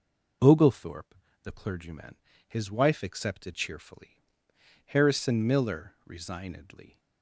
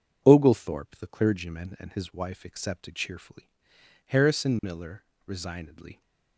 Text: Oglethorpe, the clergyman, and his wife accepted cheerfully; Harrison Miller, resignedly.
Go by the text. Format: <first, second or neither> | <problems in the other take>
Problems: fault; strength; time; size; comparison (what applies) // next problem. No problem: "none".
second | skips "and"; at 2.3 s